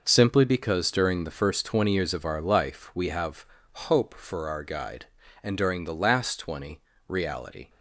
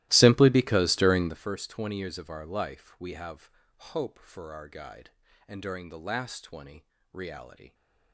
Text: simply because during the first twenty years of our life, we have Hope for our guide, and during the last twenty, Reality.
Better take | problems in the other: first | starts louder than the rest; strong; until 1.4 s; 16 dB // pauses between "have" and "Hope"; at 3.4 s; 0.44 s long; also in the first

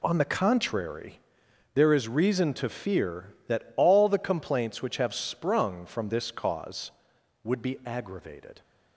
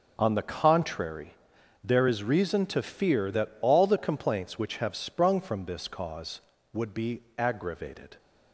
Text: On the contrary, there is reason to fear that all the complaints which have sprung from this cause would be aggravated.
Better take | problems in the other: neither | none

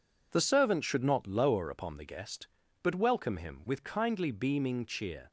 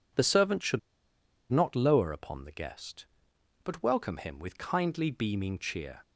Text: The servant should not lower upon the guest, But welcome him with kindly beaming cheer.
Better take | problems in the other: first | pauses between "should" and "not"; noticeable; at 0.7 s; 0.72 s long

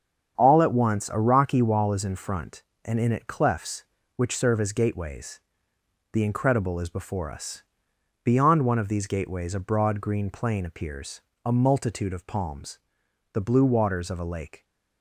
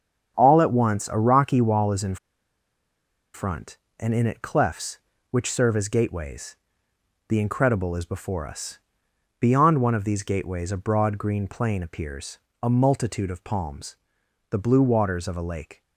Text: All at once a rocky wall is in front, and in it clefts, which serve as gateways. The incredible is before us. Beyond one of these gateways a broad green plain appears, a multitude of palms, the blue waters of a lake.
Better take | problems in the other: first | starts louder than the rest; strong; until 1.3 s; 7.5 dB; strong in the first // pauses between "in" and "front"; at 2.1 s; 1.1 s long

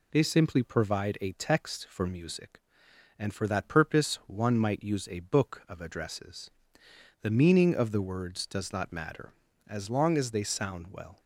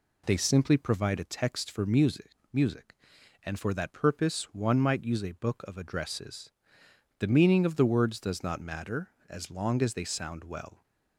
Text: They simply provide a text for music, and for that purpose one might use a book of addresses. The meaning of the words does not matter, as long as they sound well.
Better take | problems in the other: first | says "music" twice; at 2.5 s

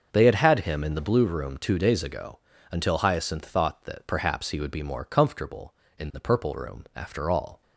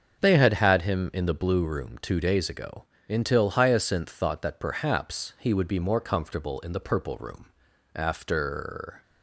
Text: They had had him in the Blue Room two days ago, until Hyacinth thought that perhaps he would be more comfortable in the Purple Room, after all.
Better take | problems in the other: first | starts louder than the rest; until 1.2 s; 7 dB; also in the first // stops before "all"; at 9.0 s

